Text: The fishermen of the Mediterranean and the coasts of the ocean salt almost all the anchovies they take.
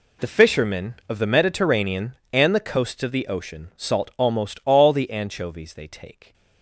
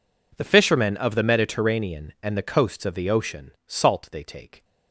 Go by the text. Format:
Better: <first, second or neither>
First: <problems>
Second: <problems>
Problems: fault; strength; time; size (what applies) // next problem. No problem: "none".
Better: first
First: none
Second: skips "almost all the anchovies"; at 4.0 s